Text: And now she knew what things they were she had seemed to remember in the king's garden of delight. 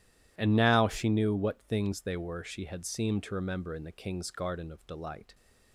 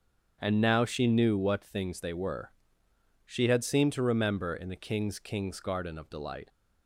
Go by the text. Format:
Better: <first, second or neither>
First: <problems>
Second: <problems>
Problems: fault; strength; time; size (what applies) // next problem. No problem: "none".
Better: first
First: none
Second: starts louder than the rest; strong; until 1.4 s; 7.5 dB // pauses between "were" and "she"; noticeable; at 2.5 s; 0.74 s long // says "king's" twice; at 5.1 s